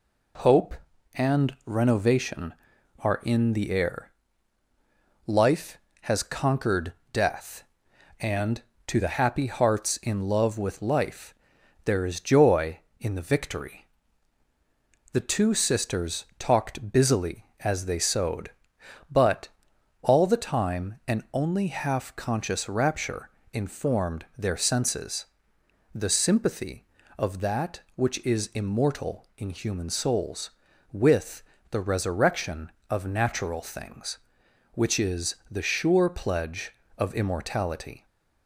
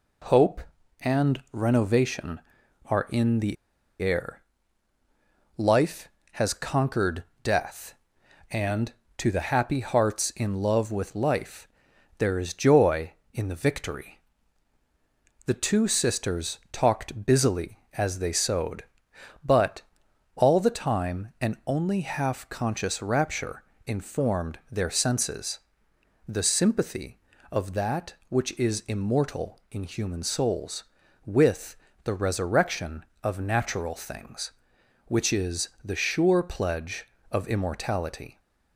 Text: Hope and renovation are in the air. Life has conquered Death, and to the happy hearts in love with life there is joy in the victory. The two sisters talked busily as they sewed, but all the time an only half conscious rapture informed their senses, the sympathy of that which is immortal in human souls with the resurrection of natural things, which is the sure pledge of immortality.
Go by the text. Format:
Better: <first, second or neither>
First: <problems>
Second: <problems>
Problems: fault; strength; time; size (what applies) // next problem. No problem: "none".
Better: first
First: pauses between "conquered" and "Death"; slight; at 6.9 s; 0.20 s long // pauses between "life" and "there"; noticeable; at 11.3 s; 0.50 s long // pauses between "but" and "all"; noticeable; at 19.4 s; 0.52 s long // pauses between "rapture" and "informed"; slight; at 23.2 s; 0.22 s long // pauses between "with" and "the"; slight; at 31.4 s; 0.26 s long // pauses between "is" and "the"; slight; at 35.3 s; 0.16 s long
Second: pauses between "the" and "air"; at 3.5 s; 0.45 s long // pauses between "conquered" and "Death"; slight; at 7.2 s; 0.20 s long // pauses between "life" and "there"; noticeable; at 11.6 s; 0.50 s long // pauses between "but" and "all"; noticeable; at 19.8 s; 0.52 s long // pauses between "rapture" and "informed"; slight; at 23.6 s; 0.22 s long // pauses between "with" and "the"; slight; at 31.7 s; 0.26 s long // pauses between "is" and "the"; slight; at 35.6 s; 0.16 s long